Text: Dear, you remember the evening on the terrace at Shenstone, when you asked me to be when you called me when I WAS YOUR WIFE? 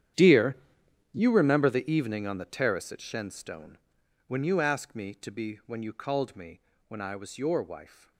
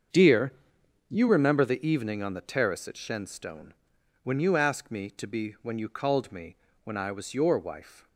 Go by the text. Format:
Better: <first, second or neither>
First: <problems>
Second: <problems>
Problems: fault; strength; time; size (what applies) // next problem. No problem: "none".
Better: second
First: gets quieter; strong; throughout; 16.5 dB // starts louder than the rest; strong; until 1.7 s; 10 dB // pauses between "me" and "when"; slight; at 6.6 s; 0.26 s long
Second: starts louder than the rest; until 1.6 s; 7 dB // pauses between "me" and "when"; slight; at 6.5 s; 0.26 s long